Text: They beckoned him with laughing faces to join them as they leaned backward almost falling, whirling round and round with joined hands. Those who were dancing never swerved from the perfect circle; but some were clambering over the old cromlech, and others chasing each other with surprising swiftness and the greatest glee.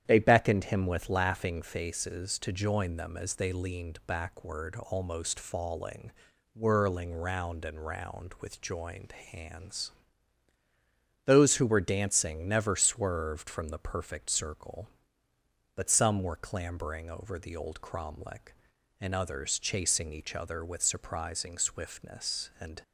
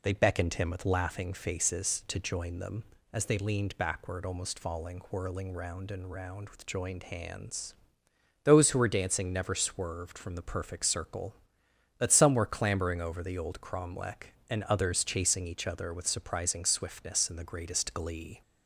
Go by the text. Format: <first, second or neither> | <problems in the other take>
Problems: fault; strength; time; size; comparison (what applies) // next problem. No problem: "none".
second | starts louder than the rest; strong; until 1.0 s; 10 dB // pauses between "joined" and "hands"; slight; at 9.1 s; 0.18 s long // stops before "the greatest glee"; at 22.8 s